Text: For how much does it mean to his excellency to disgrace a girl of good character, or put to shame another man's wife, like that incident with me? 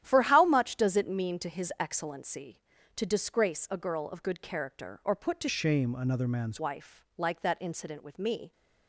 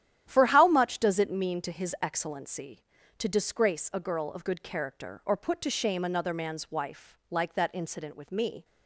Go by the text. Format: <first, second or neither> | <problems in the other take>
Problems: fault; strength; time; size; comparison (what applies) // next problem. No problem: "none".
second | starts louder than the rest; strong; until 1.0 s; 11.5 dB; strong in the second // changes voice from "shame" to "man's"; from 5.4 to 6.5 s; 1.1 s long